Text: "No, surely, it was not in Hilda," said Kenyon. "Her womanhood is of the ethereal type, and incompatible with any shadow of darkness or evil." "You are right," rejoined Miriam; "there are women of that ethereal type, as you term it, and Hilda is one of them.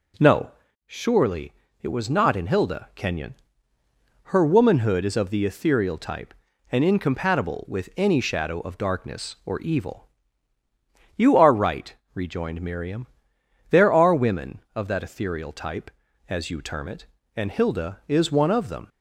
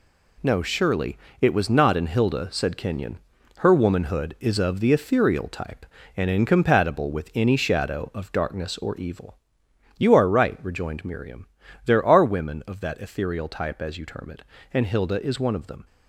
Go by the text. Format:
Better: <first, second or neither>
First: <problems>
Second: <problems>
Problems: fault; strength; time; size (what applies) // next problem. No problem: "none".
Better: second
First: skips "said"; at 2.9 s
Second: none